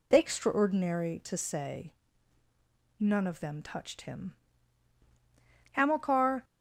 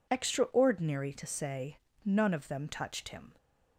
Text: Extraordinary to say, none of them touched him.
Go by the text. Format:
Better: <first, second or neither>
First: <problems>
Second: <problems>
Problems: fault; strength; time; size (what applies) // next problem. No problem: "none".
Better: second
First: goes on to say "Hamilcar"; noticeable; from 5.7 s on; 0.72 s long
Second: none